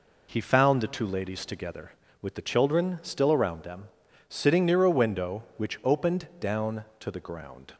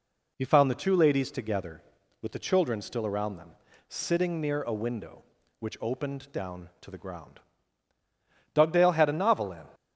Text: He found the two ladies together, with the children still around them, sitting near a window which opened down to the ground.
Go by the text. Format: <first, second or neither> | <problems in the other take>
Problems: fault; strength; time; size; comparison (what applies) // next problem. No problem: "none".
first | goes on to say "Dugdale had a novel in"; noticeable; from 8.5 s on; 1.2 s long